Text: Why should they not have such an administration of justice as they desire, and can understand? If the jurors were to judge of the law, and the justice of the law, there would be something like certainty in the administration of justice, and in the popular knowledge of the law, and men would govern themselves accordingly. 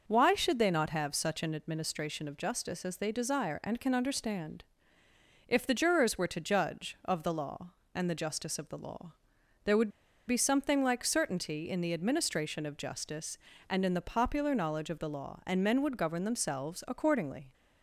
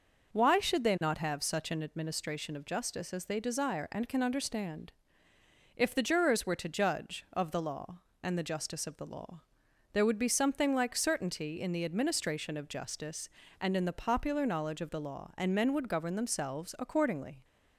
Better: second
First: pauses between "would" and "be"; at 9.8 s; 0.37 s long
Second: none

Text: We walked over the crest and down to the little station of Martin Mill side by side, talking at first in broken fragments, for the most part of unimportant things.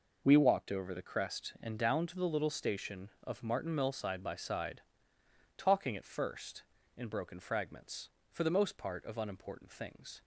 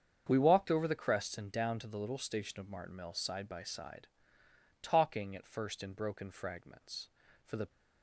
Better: first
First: none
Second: starts louder than the rest; strong; until 1.2 s; 7.5 dB // stops before "most part of unimportant things"; at 7.6 s

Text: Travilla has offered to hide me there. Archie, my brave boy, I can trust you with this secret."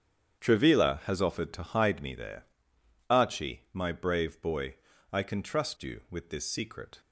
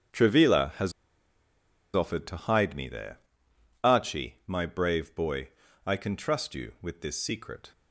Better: first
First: starts louder than the rest; strong; until 1.4 s; 8.5 dB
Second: starts louder than the rest; strong; until 2.2 s; 8.5 dB // pauses between "has" and "offered"; at 0.9 s; 1.0 s long

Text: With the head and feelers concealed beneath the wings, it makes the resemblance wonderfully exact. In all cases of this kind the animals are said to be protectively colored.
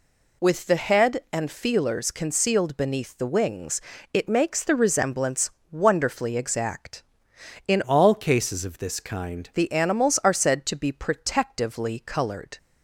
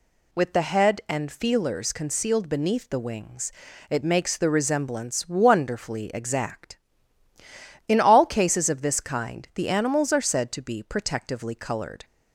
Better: second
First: pauses between "resemblance" and "wonderfully"; slight; at 5.4 s; 0.22 s long // changes voice from "all" to "kind"; from 7.8 to 9.4 s; 1.6 s long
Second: none

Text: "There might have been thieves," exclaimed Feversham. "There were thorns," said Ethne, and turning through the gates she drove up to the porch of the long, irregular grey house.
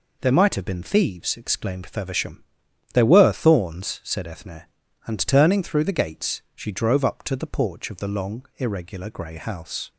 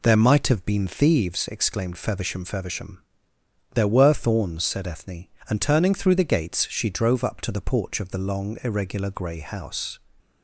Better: first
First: none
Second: says "Feversham" twice; at 2.4 s

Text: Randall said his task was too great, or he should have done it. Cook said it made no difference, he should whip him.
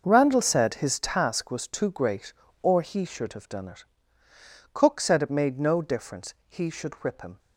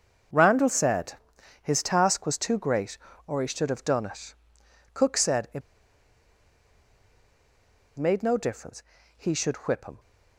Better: first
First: none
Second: starts louder than the rest; until 1.7 s; 6.5 dB // pauses between "said" and "his"; noticeable; at 1.1 s; 0.46 s long // pauses between "it" and "made"; strong; at 5.6 s; 2.3 s long

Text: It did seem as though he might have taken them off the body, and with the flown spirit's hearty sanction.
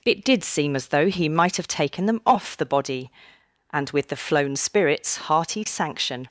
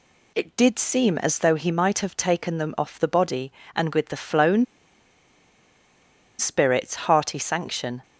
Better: first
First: none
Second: pauses between "flown" and "spirit's"; strong; at 4.6 s; 1.7 s long // pauses between "spirit's" and "hearty"; slight; at 6.9 s; 0.16 s long

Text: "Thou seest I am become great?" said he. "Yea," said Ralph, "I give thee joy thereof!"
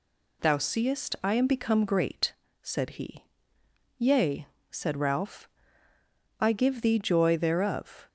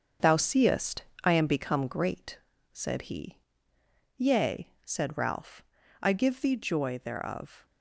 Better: first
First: none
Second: gets quieter; throughout; 7 dB // pauses between "seest" and "I"; slight; at 1.0 s; 0.20 s long

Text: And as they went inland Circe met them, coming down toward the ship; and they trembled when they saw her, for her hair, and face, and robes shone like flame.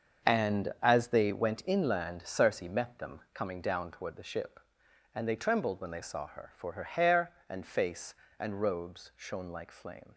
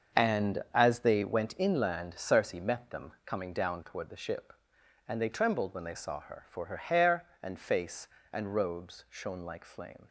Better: neither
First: starts louder than the rest; until 1.3 s; 6.5 dB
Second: starts louder than the rest; until 1.2 s; 6.5 dB

